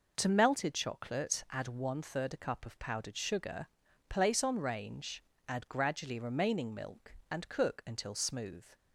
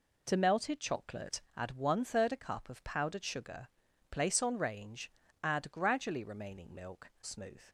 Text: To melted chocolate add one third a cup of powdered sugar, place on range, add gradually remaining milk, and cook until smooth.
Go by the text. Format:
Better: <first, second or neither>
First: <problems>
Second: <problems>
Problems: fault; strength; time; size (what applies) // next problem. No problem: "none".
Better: first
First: none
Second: pauses between "chocolate" and "add"; slight; at 1.4 s; 0.16 s long // skips "and cook until"; at 7.1 s